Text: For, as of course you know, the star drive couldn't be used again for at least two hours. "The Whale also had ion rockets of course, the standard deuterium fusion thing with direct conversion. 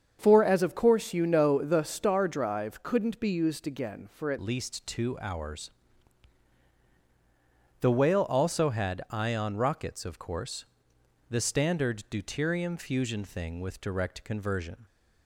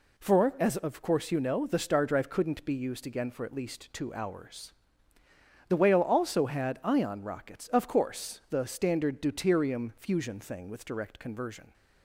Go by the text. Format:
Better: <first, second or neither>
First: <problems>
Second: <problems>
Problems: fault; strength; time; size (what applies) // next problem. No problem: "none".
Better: second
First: starts louder than the rest; strong; until 1.2 s; 7 dB // changes voice at "least"; from 4.4 s on; 10.4 s long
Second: none